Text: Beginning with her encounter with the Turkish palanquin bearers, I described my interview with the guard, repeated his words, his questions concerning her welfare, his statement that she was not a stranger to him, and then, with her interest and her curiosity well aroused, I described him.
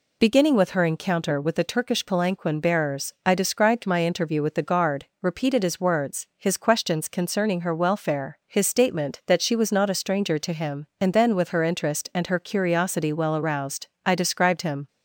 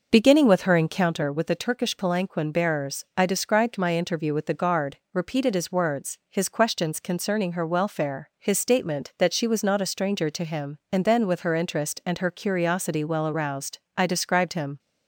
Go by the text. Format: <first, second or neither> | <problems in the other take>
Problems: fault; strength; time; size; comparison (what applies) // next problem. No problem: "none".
first | starts louder than the rest; noticeable; until 1.2 s; 6 dB